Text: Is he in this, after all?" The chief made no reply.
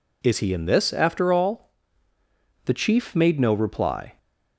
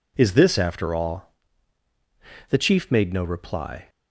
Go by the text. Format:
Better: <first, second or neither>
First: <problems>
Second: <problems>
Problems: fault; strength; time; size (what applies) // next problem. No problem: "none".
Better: first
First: none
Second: skips "he in"; at 0.3 s